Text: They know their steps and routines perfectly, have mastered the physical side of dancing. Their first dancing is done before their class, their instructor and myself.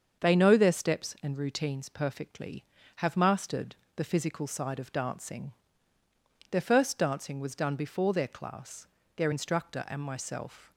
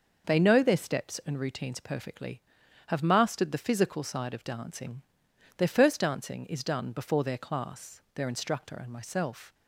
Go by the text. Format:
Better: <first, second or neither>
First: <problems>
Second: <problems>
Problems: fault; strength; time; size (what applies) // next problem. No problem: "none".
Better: second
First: starts louder than the rest; until 1.2 s; 7 dB // pauses between "mastered" and "the"; slight; at 3.7 s; 0.18 s long // says "was" for "is"; at 7.3 s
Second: none